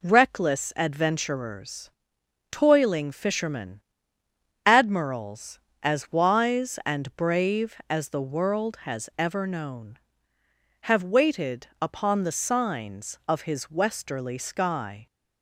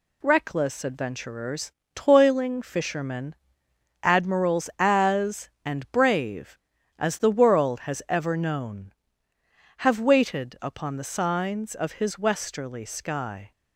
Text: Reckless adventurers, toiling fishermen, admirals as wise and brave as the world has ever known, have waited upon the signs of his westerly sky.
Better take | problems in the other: first | skips "wise"; at 5.5 s

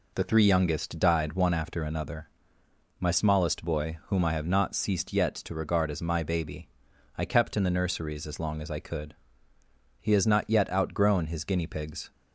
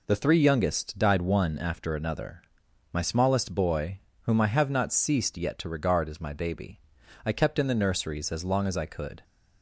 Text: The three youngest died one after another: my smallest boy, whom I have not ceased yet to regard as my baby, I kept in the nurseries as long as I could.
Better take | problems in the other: second | goes on to say "He has not yet outgrown his guinea pigs"; strong; from 9.9 s on; 2.1 s long

